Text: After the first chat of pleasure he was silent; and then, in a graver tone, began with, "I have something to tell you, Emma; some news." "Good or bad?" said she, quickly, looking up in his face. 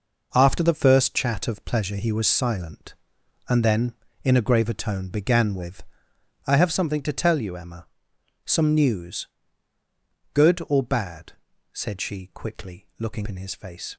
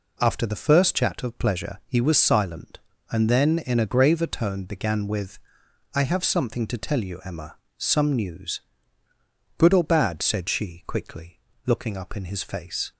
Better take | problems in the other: second | skips "up"; at 13.2 s

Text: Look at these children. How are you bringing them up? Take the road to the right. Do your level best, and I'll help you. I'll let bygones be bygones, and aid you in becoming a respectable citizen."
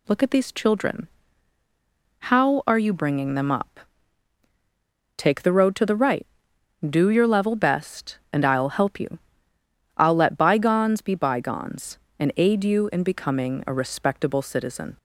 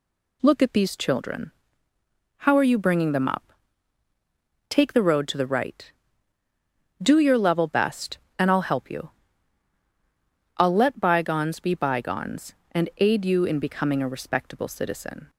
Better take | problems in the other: neither | none

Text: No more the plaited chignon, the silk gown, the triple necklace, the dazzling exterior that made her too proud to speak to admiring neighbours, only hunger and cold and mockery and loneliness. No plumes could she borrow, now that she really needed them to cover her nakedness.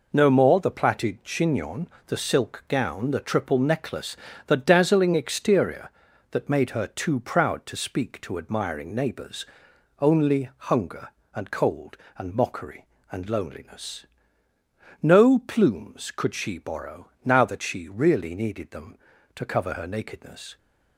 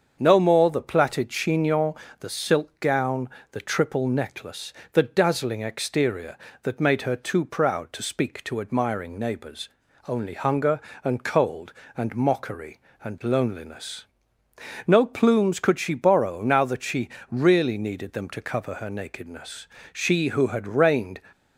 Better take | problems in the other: first | starts louder than the rest; until 1.2 s; 7 dB // pauses between "she" and "really"; slight; at 17.0 s; 0.20 s long // goes on to say "She who had reigned"; noticeable; from 19.9 s on; 1.2 s long

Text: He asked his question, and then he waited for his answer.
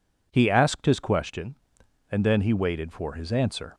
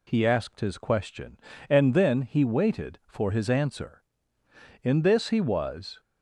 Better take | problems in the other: first | goes on to say "In this he was"; noticeable; from 4.8 s on; 1.1 s long

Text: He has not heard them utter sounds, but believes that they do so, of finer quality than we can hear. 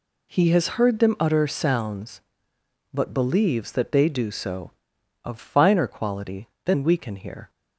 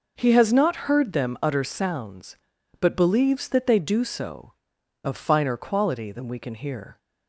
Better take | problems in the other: second | skips "not"; at 0.7 s

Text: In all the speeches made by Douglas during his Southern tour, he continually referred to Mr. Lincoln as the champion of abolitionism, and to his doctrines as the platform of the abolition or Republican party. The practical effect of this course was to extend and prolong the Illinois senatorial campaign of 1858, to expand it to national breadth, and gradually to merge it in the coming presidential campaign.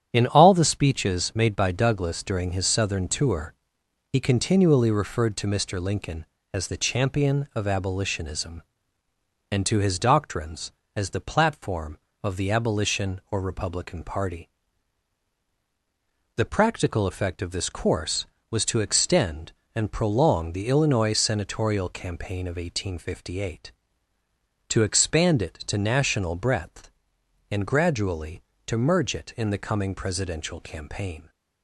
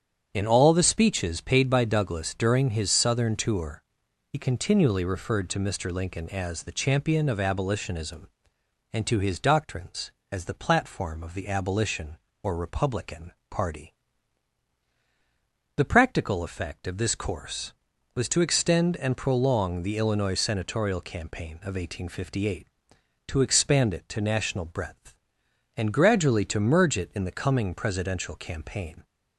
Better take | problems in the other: first | starts louder than the rest; strong; until 1.3 s; 8.5 dB; strong in the first // says "paid" for "made"; at 1.4 s // pauses between "Republican" and "party"; slight; at 13.3 s; 0.18 s long

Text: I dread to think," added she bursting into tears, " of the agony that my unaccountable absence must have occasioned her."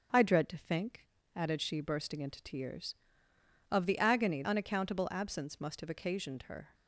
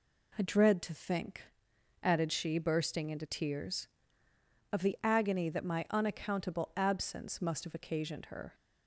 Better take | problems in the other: second | skips "that my"; at 4.4 s

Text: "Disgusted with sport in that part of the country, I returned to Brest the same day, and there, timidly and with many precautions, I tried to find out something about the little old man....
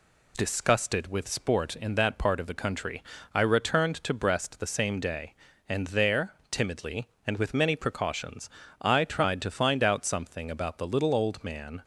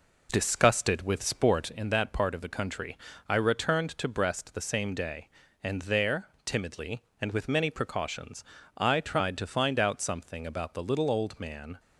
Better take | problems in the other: first | starts louder than the rest; noticeable; until 1.7 s; 4 dB

